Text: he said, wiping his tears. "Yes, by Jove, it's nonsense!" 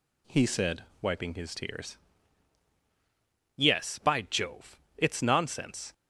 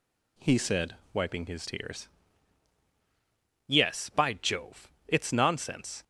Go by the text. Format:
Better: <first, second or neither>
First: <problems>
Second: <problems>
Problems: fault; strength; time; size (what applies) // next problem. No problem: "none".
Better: neither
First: none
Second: none